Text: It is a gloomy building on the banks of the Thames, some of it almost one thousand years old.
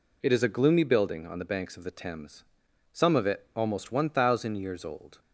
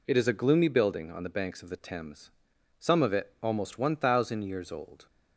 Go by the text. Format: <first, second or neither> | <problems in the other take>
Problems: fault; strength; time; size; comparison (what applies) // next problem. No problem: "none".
neither | none